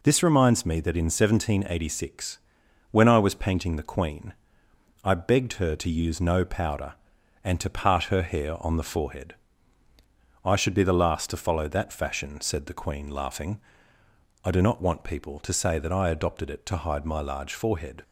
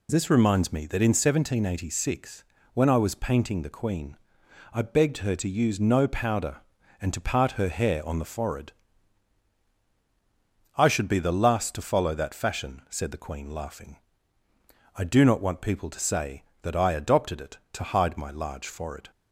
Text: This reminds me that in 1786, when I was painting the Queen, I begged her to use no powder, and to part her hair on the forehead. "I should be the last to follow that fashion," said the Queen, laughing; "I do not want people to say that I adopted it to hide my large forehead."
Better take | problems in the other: neither | none

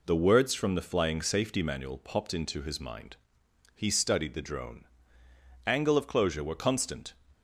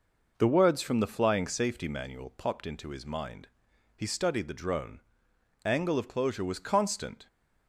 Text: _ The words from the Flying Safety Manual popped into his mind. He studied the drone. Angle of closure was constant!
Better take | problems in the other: second | says "were" for "was"; at 6.4 s

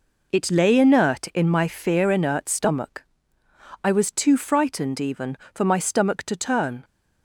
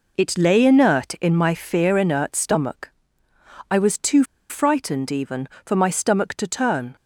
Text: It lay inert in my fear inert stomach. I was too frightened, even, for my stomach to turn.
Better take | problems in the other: first | pauses between "too" and "frightened"; slight; at 4.2 s; 0.26 s long

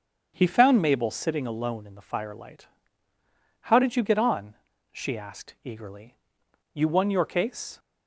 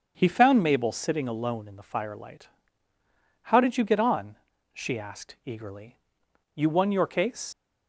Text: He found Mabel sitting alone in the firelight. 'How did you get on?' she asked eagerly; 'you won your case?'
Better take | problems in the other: first | starts louder than the rest; until 1.1 s; 7 dB; strong in the first // leaves "case" unfinished; at 7.5 s; 75 ms

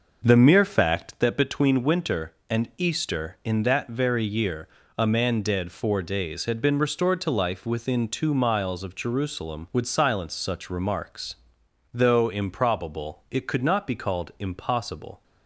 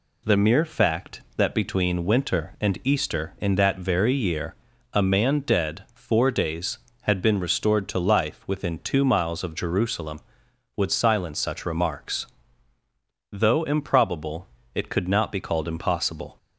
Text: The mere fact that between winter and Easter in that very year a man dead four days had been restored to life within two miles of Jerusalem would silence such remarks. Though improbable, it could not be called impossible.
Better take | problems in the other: second | starts louder than the rest; noticeable; until 1.2 s; 6 dB // pauses between "year" and "a"; slight; at 4.6 s; 0.28 s long; also in the second

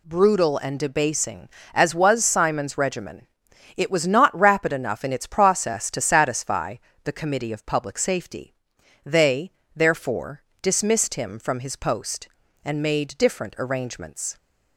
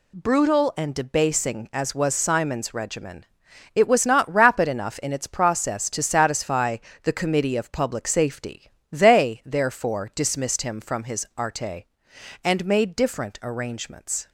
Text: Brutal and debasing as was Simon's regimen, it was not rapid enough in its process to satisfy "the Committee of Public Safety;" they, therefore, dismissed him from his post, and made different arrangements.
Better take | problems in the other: first | pauses between "satisfy" and "the"; slight; at 6.7 s; 0.26 s long; slight in the first // says "arte" for "post"; at 11.3 s

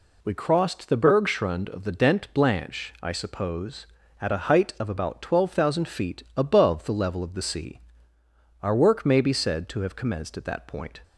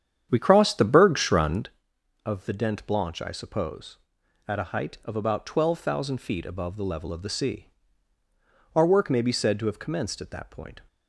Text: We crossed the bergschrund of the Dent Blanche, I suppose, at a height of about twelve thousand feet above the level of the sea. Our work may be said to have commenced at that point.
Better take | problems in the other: first | starts louder than the rest; strong; until 1.7 s; 9 dB

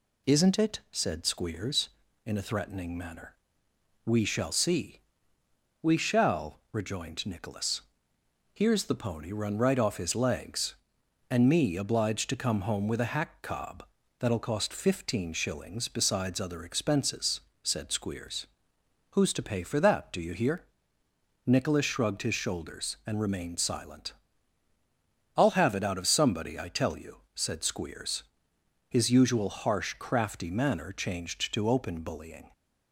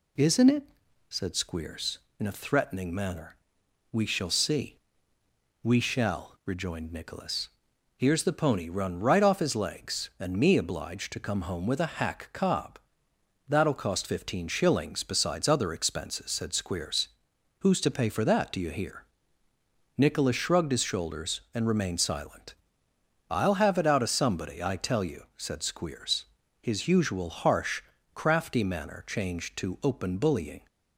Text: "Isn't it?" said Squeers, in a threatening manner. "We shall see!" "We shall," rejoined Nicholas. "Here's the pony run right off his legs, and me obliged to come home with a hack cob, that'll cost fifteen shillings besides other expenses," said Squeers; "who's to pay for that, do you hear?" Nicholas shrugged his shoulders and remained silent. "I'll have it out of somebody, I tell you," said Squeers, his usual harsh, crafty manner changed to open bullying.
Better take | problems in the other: neither | none

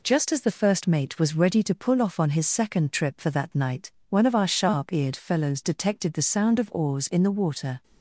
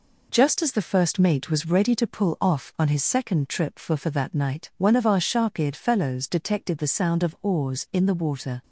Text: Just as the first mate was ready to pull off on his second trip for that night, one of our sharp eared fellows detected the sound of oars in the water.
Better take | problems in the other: first | says "for" twice; at 3.9 s

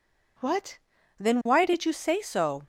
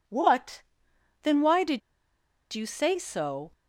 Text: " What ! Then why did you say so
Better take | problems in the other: first | pauses between "did" and "you"; noticeable; at 1.8 s; 0.73 s long

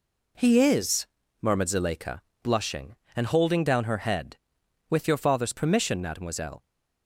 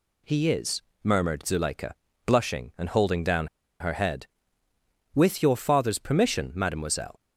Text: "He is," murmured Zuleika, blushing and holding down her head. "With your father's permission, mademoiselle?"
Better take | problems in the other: first | pauses between "down" and "her"; slight; at 3.4 s; 0.33 s long

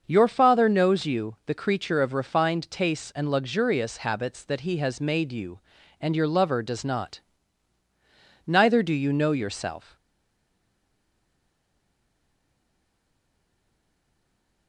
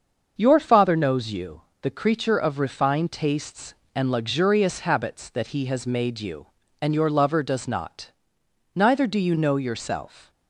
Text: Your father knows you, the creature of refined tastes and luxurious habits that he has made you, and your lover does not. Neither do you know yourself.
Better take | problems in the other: second | starts louder than the rest; until 1.0 s; 6.5 dB; also in the second // stays silent after the last word; strong; from 9.9 s on; 4.7 s long

